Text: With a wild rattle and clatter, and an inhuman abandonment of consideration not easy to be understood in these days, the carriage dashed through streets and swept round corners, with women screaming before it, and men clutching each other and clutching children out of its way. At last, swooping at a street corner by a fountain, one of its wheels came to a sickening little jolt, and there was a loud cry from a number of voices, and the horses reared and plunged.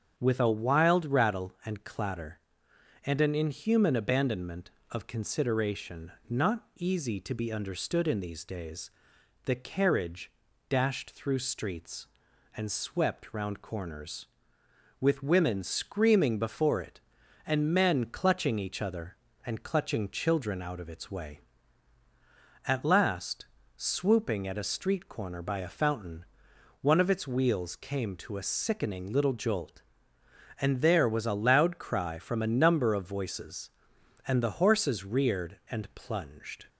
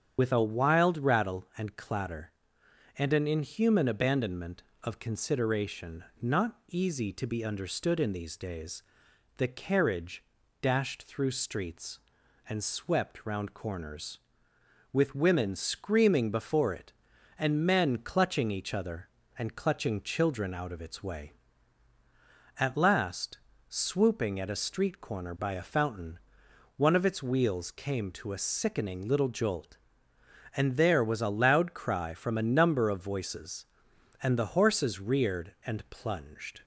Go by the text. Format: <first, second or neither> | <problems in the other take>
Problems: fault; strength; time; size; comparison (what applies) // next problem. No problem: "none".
first | loses the start of "With"; at 0.1 s; 80 ms // starts louder than the rest; strong; until 1.1 s; 8 dB; strong in the first // pauses between "consideration" and "not"; slight; at 6.0 s; 0.16 s long; slight in the first // pauses between "carriage" and "dashed"; at 10.2 s; 0.40 s long; also in the first